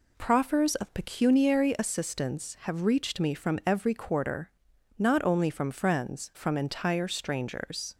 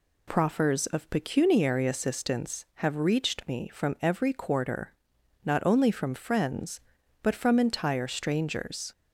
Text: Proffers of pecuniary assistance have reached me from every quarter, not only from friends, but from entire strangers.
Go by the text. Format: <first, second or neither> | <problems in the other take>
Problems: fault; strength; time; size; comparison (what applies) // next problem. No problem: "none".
second | skips "but"; at 6.3 s